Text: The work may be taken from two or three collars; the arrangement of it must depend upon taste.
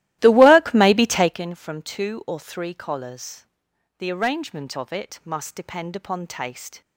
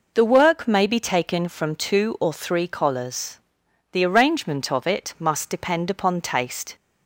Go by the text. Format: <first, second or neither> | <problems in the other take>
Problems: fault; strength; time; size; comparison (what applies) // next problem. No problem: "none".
second | starts louder than the rest; strong; until 1.4 s; 15.5 dB